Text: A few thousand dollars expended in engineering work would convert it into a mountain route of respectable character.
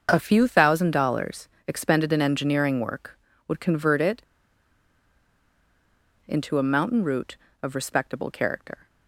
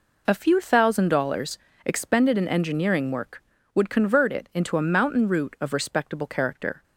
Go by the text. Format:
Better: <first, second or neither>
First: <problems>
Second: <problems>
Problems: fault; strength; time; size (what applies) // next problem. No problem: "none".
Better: second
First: starts louder than the rest; until 1.1 s; 6.5 dB // pauses between "dollars" and "expended"; slight; at 1.4 s; 0.20 s long // pauses between "it" and "into"; strong; at 4.2 s; 2.0 s long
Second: pauses between "dollars" and "expended"; slight; at 1.5 s; 0.26 s long